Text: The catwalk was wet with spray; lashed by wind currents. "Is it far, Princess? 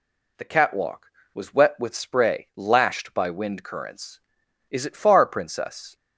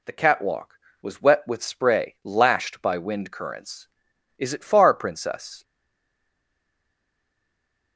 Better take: first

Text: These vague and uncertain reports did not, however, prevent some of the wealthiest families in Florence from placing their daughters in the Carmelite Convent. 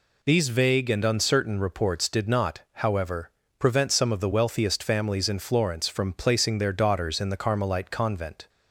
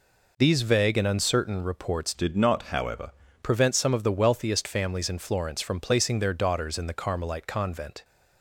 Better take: first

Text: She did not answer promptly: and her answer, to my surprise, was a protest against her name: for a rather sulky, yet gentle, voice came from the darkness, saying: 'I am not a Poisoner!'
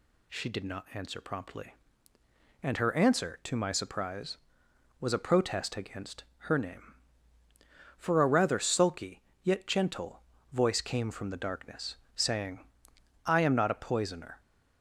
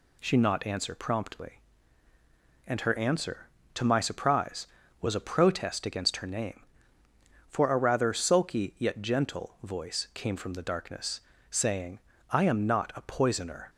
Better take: first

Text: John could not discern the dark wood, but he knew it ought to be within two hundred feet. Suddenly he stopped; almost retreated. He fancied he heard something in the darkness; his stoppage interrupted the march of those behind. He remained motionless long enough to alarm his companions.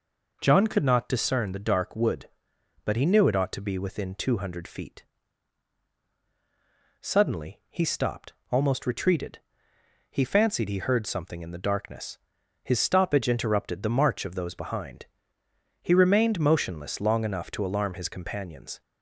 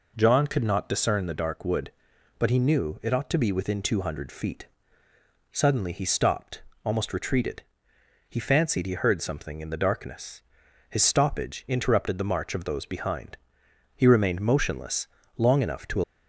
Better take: first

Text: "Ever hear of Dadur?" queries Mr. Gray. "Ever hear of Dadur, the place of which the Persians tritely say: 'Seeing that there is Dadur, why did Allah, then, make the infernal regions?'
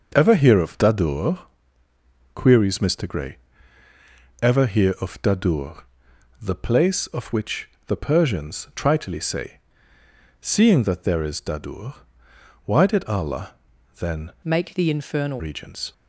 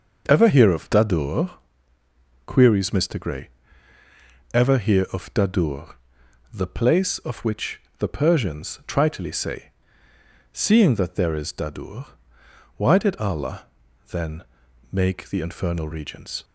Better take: second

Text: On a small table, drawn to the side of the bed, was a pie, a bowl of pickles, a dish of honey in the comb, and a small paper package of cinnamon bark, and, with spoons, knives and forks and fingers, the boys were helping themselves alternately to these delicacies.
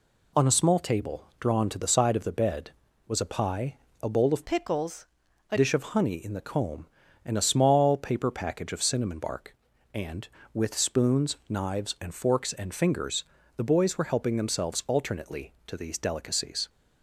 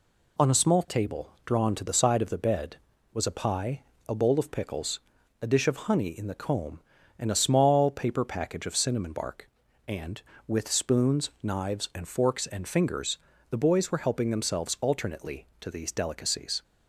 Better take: second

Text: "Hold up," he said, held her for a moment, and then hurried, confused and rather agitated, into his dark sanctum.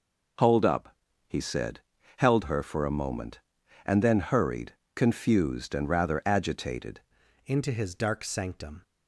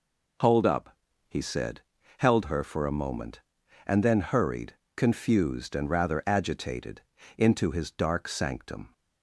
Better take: second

